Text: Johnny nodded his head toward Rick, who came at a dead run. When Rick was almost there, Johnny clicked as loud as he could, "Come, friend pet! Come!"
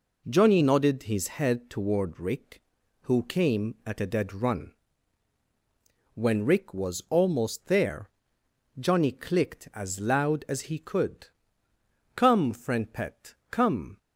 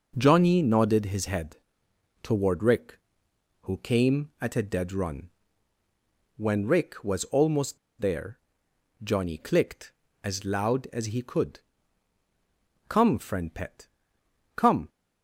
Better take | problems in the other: first | pauses between "head" and "toward"; noticeable; at 1.5 s; 0.66 s long // pauses between "almost" and "there"; slight; at 7.7 s; 0.22 s long

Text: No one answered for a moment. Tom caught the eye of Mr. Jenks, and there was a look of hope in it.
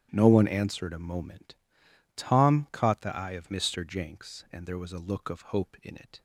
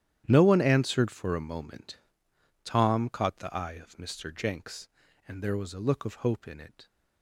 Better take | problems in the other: second | starts louder than the rest; strong; until 1.1 s; 11.5 dB; strong in the second // skips "for"; at 0.9 s

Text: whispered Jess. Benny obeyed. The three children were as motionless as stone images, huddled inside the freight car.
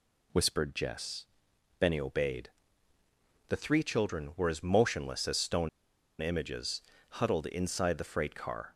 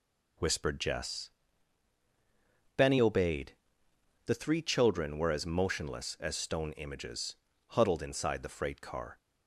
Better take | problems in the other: second | pauses between "stone" and "images"; noticeable; at 5.6 s; 0.52 s long

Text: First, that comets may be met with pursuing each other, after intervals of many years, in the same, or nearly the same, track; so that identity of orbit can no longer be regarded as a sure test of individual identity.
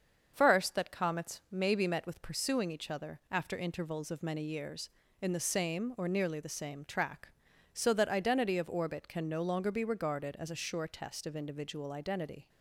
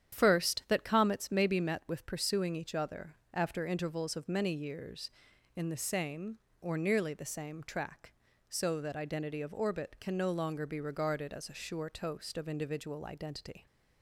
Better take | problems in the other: first | starts louder than the rest; strong; until 1.2 s; 9.5 dB; also in the first // says "toast" for "test"; at 11.8 s

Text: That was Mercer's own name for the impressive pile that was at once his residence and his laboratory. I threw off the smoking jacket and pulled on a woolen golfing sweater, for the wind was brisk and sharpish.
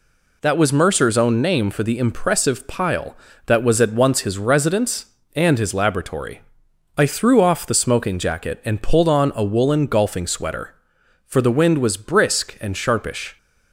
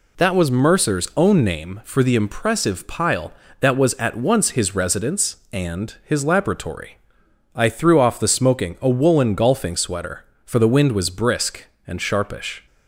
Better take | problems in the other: first | skips "jacket and pulled on"; at 8.7 s

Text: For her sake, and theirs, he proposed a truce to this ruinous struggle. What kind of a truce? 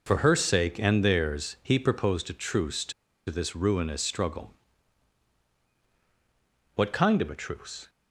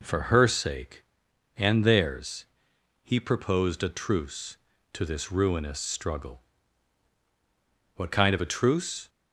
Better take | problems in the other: second | pauses between "to" and "this"; at 2.9 s; 0.36 s long

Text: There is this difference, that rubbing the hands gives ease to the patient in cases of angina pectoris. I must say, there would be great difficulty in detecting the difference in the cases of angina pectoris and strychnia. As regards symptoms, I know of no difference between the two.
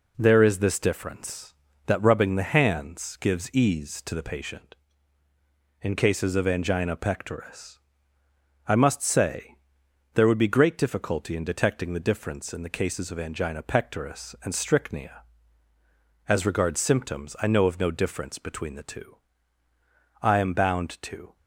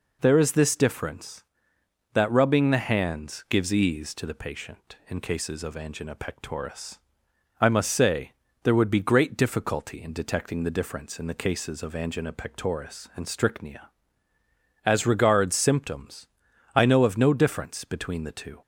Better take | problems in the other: second | goes on to say "I am bound to"; noticeable; from 20.2 s on; 1.1 s long

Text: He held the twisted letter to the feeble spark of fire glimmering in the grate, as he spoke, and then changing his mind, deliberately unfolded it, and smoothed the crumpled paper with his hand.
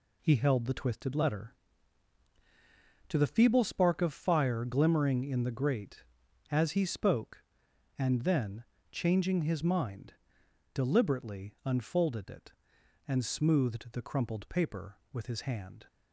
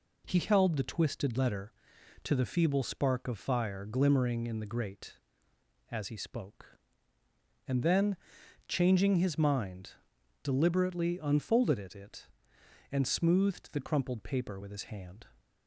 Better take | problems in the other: first | pauses between "then" and "changing"; noticeable; at 8.1 s; 0.52 s long; slight in the first // says "it" twice; at 11.9 s

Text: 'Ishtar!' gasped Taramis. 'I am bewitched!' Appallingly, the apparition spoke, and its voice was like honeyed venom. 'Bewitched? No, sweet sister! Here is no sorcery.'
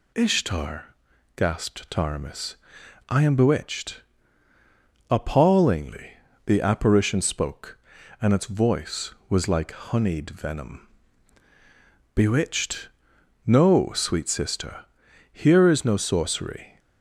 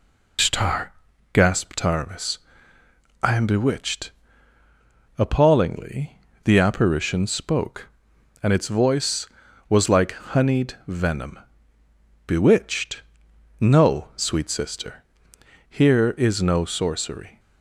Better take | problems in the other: first | loses the start of "Ishtar"; at 0.3 s; 155 ms

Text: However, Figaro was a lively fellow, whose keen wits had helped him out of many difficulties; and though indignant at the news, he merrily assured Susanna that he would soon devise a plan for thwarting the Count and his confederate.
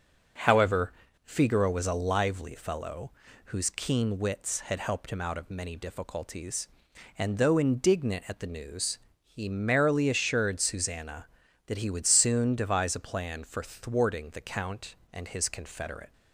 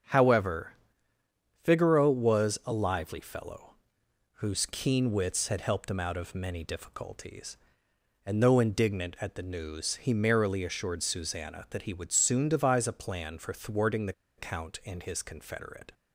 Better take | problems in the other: first | starts louder than the rest; strong; until 1.9 s; 7 dB; also in the first // pauses between "the" and "Count"; slight; at 14.1 s; 0.26 s long

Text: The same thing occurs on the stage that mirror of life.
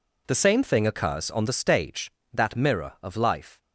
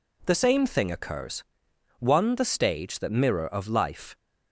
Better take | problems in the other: first | says "one" for "on"; at 1.9 s

